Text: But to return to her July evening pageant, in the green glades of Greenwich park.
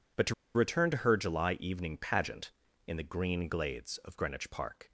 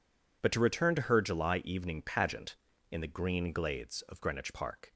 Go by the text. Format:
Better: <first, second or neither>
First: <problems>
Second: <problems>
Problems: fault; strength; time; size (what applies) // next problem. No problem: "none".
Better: second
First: pauses between "to" and "return"; slight; at 0.3 s; 0.21 s long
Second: none